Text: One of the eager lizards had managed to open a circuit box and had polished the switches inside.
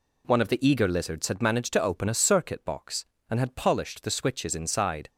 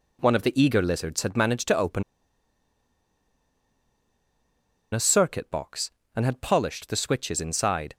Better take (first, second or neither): first